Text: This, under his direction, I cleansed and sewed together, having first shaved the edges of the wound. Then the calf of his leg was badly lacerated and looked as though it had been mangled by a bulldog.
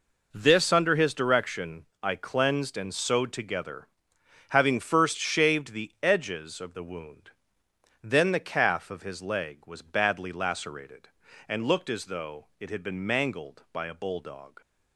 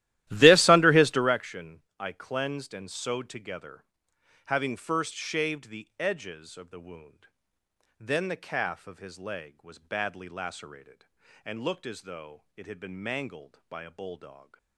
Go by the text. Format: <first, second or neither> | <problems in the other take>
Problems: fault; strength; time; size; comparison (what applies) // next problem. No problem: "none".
first | starts louder than the rest; strong; until 1.4 s; 15 dB